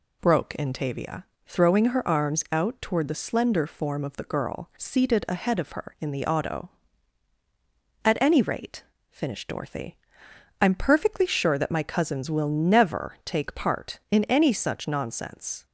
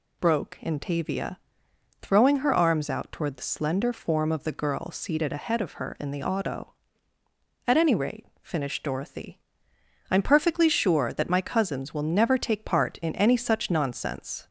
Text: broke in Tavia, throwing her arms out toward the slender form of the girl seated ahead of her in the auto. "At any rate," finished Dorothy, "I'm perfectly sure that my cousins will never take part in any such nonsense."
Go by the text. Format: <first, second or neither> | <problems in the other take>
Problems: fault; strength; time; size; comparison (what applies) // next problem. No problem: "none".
neither | none